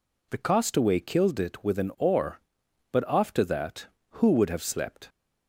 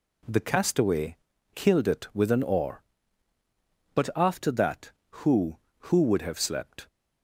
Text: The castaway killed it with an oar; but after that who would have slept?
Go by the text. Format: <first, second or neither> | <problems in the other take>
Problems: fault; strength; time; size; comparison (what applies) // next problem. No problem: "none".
first | pauses between "castaway" and "killed"; at 1.1 s; 0.38 s long // says "who" twice; at 5.8 s